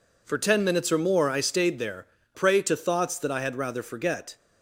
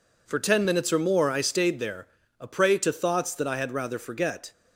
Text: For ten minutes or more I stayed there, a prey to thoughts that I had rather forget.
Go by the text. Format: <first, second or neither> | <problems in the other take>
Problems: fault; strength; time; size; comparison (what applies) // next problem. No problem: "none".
second | skips "a"; at 2.2 s